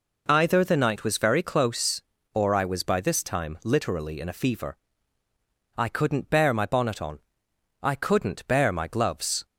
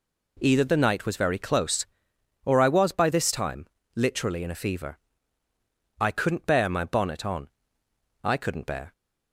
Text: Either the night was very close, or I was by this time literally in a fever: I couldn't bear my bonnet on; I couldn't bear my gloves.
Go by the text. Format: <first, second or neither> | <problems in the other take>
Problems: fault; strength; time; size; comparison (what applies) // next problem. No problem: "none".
first | pauses between "time" and "literally"; slight; at 3.6 s; 0.28 s long // stops before "my gloves"; at 8.9 s